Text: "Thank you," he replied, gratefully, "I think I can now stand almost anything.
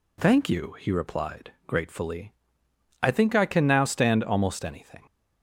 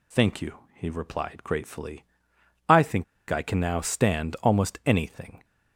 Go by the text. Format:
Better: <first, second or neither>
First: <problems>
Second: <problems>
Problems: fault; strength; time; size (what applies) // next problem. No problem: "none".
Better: first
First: none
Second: pauses between "think" and "I"; slight; at 3.0 s; 0.25 s long